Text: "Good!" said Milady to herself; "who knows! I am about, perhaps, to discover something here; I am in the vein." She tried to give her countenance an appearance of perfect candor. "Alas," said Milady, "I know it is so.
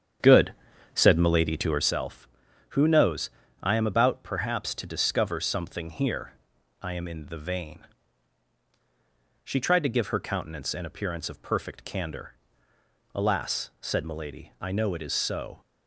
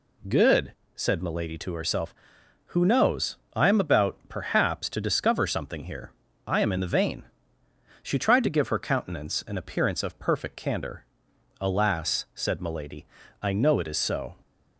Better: second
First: starts louder than the rest; strong; until 1.9 s; 8 dB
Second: none

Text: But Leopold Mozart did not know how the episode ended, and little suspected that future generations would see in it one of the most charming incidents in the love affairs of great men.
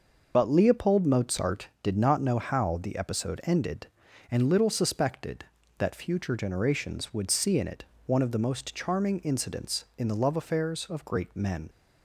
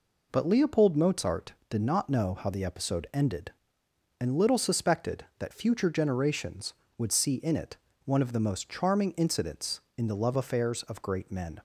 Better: second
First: loses the start of "But"; at 0.3 s; 45 ms // starts louder than the rest; noticeable; until 1.3 s; 6 dB // pauses between "it" and "one"; slight; at 7.8 s; 0.22 s long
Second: pauses between "it" and "one"; slight; at 7.7 s; 0.28 s long

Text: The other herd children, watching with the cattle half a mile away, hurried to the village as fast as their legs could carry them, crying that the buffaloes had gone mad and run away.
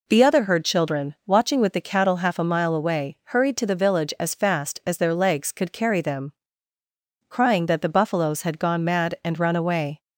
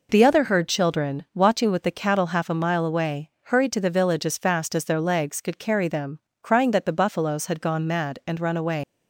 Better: first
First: none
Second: leaves "away" unfinished; at 8.8 s; 145 ms

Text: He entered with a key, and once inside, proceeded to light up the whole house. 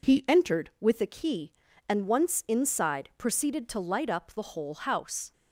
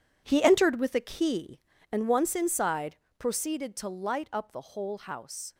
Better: first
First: none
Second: gets quieter; strong; throughout; 11.5 dB

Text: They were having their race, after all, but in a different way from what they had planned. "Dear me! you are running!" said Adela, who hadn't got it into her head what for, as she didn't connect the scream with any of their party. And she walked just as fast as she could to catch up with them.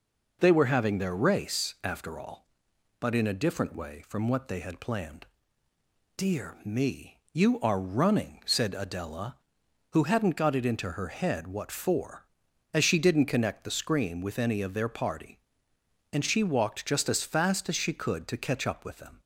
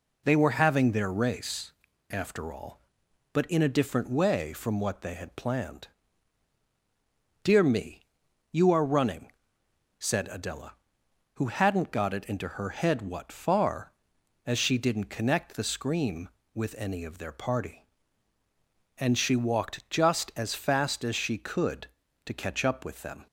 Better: first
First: none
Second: says "far" for "for"; at 13.3 s

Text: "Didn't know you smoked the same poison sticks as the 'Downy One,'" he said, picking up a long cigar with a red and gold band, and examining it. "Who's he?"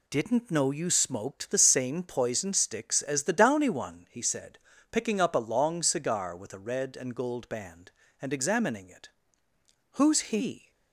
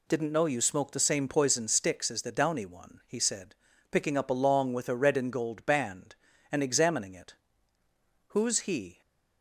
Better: first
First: none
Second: skips "cigar"; at 4.7 s

